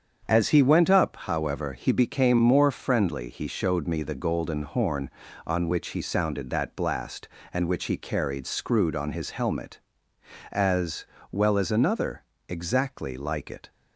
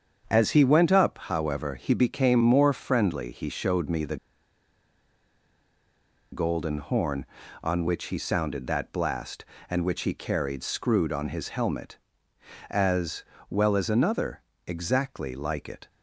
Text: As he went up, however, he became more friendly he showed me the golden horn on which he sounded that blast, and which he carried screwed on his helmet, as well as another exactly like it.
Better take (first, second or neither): first